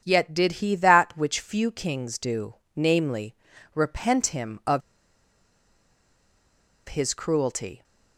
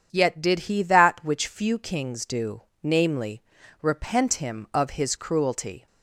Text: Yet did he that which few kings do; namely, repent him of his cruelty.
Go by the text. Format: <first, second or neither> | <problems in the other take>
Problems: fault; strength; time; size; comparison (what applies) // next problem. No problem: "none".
second | starts louder than the rest; strong; until 1.0 s; 8 dB; strong in the second // pauses between "of" and "his"; strong; at 4.8 s; 2.0 s long